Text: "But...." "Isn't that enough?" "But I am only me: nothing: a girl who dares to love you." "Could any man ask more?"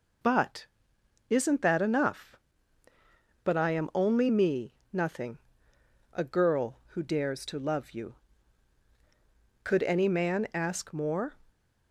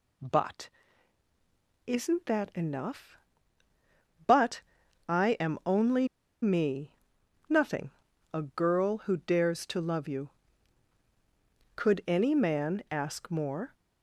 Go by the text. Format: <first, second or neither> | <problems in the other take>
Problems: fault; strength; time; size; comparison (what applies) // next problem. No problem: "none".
first | pauses between "But" and "I"; noticeable; at 4.6 s; 0.48 s long // pauses between "only" and "me"; slight; at 6.0 s; 0.35 s long